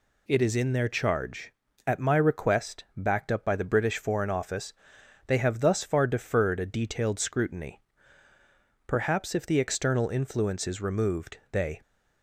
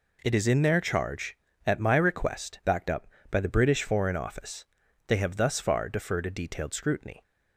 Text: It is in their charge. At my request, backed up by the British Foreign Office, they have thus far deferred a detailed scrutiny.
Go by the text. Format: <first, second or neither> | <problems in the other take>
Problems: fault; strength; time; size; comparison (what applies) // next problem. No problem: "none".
second | goes on to say "Perhaps if the external influence is removed they"; strong; from 8.8 s on; 2.9 s long